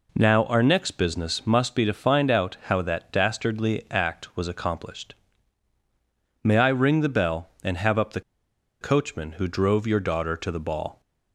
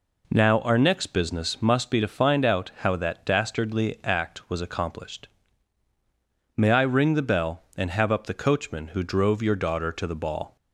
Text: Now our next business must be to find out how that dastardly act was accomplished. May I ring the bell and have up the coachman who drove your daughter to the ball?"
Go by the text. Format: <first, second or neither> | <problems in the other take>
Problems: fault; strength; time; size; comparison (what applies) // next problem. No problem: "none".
second | pauses between "the" and "coachman"; noticeable; at 8.2 s; 0.60 s long